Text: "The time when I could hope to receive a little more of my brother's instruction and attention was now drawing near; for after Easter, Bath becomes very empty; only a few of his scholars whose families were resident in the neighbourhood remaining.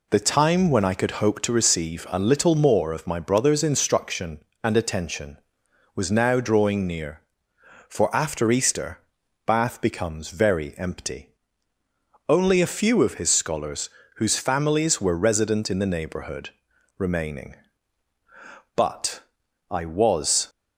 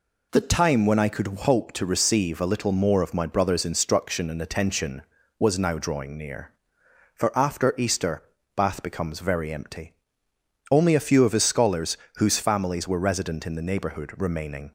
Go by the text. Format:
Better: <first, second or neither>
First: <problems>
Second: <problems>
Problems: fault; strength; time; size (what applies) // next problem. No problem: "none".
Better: second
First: pauses between "scholars" and "whose"; slight; at 13.9 s; 0.26 s long // pauses between "neighbourhood" and "remaining"; at 16.5 s; 0.44 s long // goes on to say "But I was"; strong; from 18.7 s on; 1.7 s long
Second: pauses between "scholars" and "whose"; slight; at 11.9 s; 0.20 s long